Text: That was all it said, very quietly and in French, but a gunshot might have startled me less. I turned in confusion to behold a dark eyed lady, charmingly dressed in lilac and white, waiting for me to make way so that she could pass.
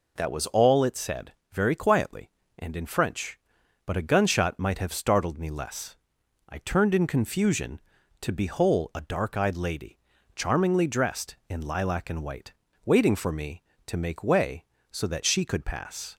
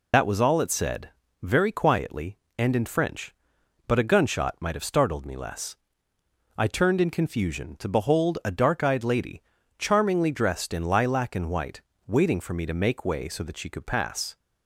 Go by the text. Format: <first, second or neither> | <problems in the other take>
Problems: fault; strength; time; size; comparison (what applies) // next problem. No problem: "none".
first | loses the start of "That"; at 0.1 s; 70 ms